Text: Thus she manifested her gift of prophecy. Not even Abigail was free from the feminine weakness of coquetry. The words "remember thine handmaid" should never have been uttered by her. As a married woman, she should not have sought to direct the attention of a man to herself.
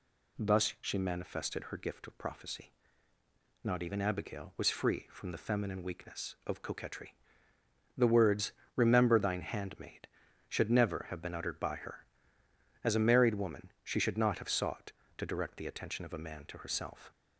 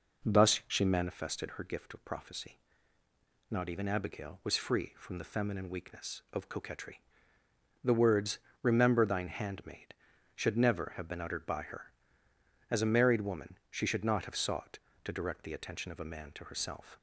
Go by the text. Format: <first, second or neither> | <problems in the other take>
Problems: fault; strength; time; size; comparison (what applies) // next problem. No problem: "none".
first | starts louder than the rest; noticeable; until 1.2 s; 4.5 dB // pauses between "words" and "remember"; slight; at 8.3 s; 0.22 s long; slight in the first